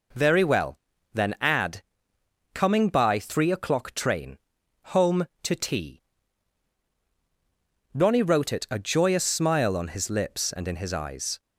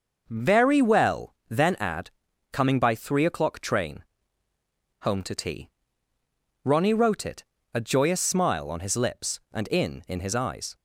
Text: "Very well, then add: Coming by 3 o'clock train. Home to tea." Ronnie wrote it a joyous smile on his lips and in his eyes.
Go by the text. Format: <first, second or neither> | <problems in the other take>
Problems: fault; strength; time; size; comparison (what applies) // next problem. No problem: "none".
first | pauses between "it" and "a"; slight; at 7.4 s; 0.28 s long // says "in" twice; at 10.0 s